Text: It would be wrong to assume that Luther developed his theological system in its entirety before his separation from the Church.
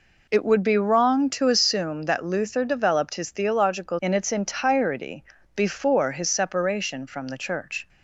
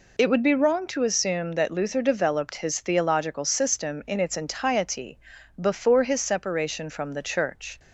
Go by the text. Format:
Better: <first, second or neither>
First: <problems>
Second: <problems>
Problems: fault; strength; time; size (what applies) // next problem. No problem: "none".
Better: second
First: skips "system"; at 3.9 s // pauses between "entirety" and "before"; slight; at 5.2 s; 0.32 s long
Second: pauses between "entirety" and "before"; at 5.1 s; 0.42 s long